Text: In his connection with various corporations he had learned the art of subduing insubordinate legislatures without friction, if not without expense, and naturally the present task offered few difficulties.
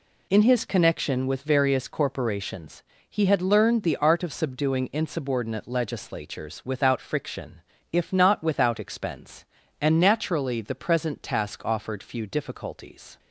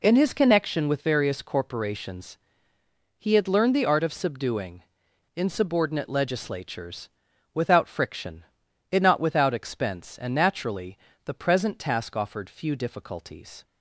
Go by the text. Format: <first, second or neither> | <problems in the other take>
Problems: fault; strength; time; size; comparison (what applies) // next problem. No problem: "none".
first | pauses between "corporations" and "he"; noticeable; at 2.3 s; 0.84 s long; slight in the first // pauses between "subduing" and "insubordinate"; noticeable; at 4.8 s; 0.51 s long // pauses between "legislatures" and "without"; noticeable; at 7.0 s; 0.46 s long // says "it" for "if"; at 8.9 s // pauses between "naturally" and "the"; slight; at 10.9 s; 0.28 s long